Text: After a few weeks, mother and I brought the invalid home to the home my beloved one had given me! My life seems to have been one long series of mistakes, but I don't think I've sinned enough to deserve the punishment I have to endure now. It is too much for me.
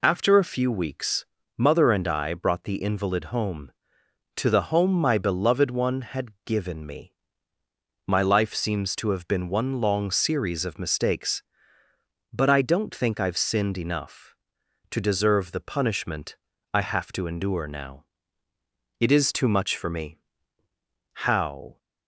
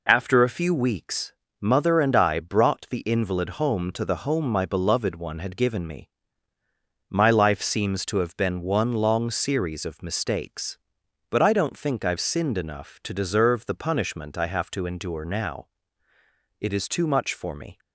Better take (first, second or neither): second